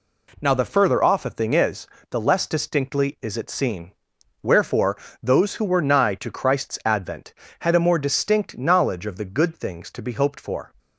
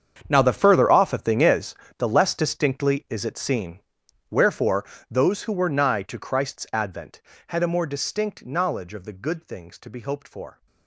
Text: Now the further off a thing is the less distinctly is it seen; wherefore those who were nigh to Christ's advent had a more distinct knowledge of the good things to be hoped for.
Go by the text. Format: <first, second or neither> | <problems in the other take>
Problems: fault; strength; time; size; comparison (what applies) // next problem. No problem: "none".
first | gets quieter; strong; throughout; 15.5 dB // pauses between "is" and "the"; slight; at 1.7 s; 0.24 s long; slight in the first // pauses between "wherefore" and "those"; slight; at 4.8 s; 0.28 s long; slight in the first